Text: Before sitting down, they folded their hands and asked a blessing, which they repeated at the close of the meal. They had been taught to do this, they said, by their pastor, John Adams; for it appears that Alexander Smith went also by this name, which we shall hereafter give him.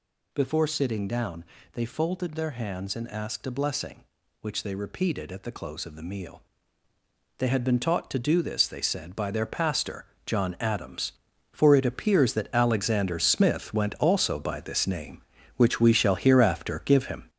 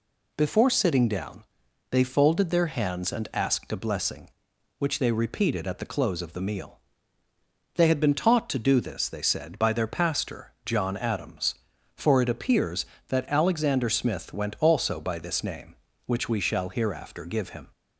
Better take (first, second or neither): second